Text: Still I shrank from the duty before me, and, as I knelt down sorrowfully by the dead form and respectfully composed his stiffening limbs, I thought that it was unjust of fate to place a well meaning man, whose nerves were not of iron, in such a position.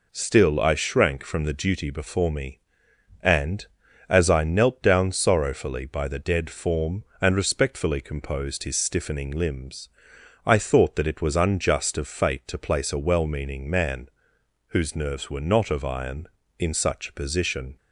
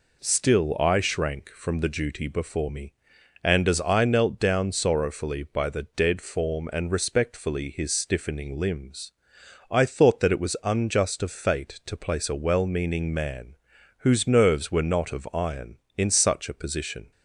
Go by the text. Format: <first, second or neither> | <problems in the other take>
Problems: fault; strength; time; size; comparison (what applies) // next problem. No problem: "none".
first | skips "composed"; at 7.7 s